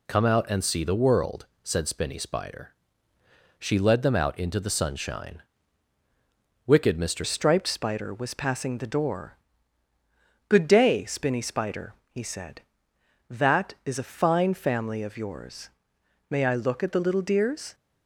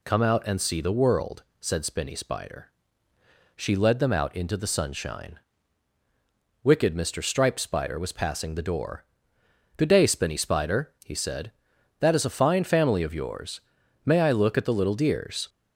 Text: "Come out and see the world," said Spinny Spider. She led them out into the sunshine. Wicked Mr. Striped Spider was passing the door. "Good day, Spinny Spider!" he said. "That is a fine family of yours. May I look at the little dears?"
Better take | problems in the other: second | changes voice at "Striped"; from 7.2 s on; 10.5 s long

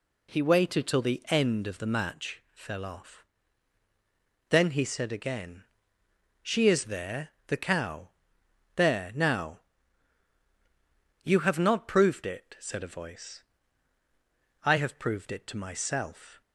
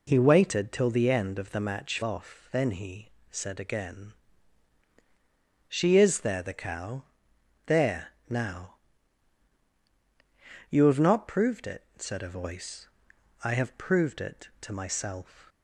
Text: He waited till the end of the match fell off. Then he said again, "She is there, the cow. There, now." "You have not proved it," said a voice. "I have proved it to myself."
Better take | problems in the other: first | skips "fell"; at 2.0 s // pauses between "he" and "said"; slight; at 3.0 s; 0.22 s long

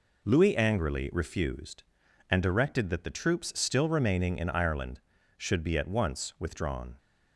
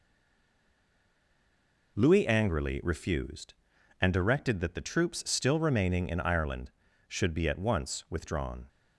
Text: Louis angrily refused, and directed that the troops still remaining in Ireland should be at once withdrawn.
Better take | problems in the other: first | stays silent before the first word; noticeable; until 1.9 s; 1.9 s long

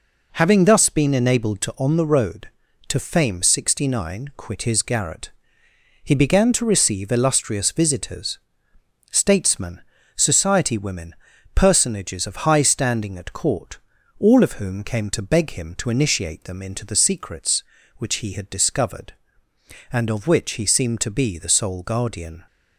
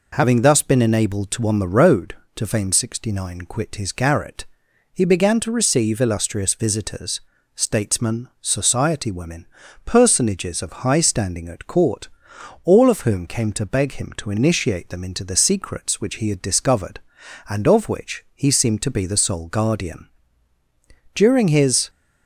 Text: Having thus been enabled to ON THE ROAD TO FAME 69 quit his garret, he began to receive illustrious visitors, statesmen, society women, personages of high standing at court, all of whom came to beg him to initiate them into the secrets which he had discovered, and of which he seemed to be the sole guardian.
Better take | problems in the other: first | goes on to say "During his"; noticeable; from 21.1 s on; 0.74 s long

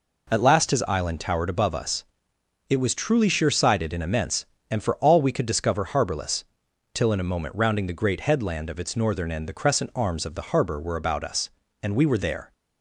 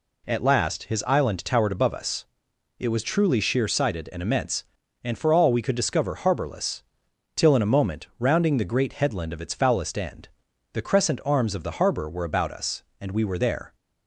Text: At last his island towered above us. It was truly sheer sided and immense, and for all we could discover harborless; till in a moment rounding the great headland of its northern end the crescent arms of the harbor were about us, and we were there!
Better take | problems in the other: first | says "foulest" for "northern"; at 9.5 s // pauses between "end" and "the"; at 10.2 s; 0.44 s long

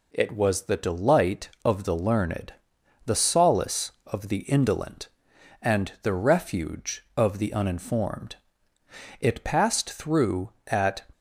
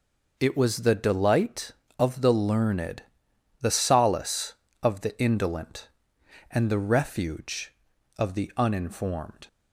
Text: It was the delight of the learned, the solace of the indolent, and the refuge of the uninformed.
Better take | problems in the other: second | goes on to say "It passed through at"; strong; from 9.2 s on; 1.8 s long

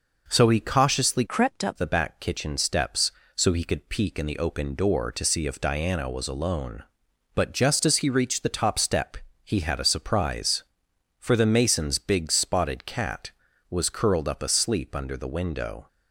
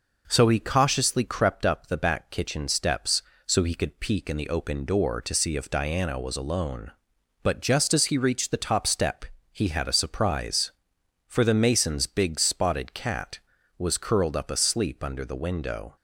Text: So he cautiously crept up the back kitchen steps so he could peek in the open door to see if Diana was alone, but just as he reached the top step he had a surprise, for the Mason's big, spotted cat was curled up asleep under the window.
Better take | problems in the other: second | changes voice from "crept" to "up"; from 1.2 to 1.7 s; 0.5 s long // pauses between "step" and "he"; slight; at 9.1 s; 0.26 s long; slight in the second

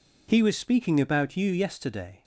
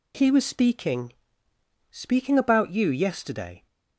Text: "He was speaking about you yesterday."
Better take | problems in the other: first | says "speaking" twice; at 1.9 s

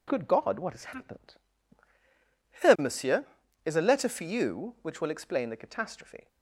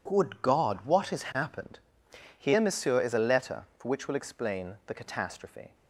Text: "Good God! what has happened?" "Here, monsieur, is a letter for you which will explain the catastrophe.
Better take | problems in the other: first | skips "you"; at 3.8 s

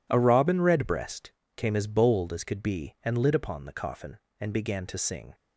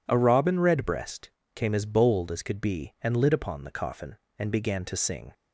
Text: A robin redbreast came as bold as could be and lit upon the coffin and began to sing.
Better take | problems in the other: second | gets quieter; strong; throughout; 12.5 dB // pauses between "redbreast" and "came"; slight; at 1.3 s; 0.24 s long; slight in the second

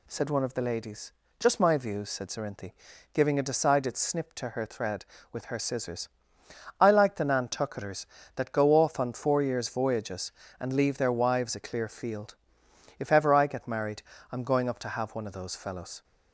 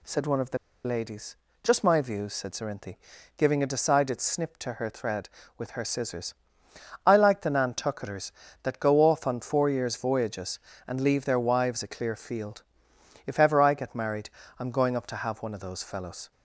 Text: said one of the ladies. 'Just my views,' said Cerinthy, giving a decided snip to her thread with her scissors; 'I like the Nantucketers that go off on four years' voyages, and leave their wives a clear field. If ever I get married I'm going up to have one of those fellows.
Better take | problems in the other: first | pauses between "the" and "ladies"; slight; at 0.5 s; 0.27 s long // pauses between "married" and "I'm"; slight; at 14.3 s; 0.28 s long; slight in the first

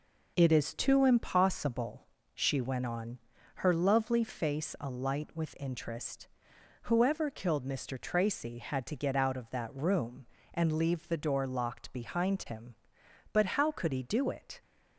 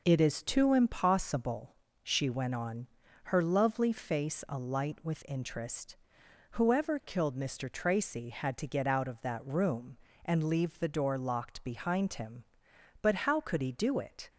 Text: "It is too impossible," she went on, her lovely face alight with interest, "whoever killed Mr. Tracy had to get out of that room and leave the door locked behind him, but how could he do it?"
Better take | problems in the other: neither | none

